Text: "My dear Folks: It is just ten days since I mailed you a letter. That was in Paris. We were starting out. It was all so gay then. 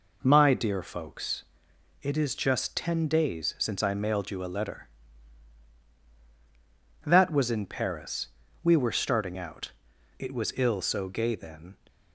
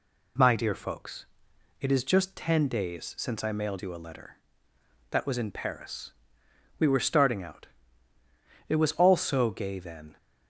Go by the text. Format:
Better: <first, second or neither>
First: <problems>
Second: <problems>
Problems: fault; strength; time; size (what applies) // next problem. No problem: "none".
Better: second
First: says "ill" for "all"; at 10.5 s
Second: none